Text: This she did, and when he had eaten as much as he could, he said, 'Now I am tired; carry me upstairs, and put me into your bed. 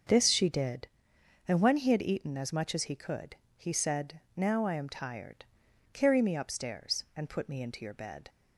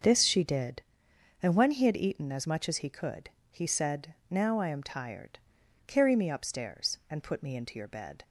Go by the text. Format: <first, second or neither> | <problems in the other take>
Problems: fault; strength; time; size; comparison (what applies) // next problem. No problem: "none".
neither | starts louder than the rest; the same in both